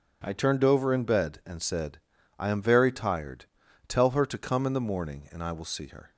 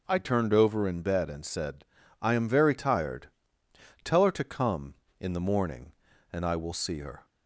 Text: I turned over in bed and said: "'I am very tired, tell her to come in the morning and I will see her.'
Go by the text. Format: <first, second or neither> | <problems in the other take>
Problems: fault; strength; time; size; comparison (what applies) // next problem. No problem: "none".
neither | none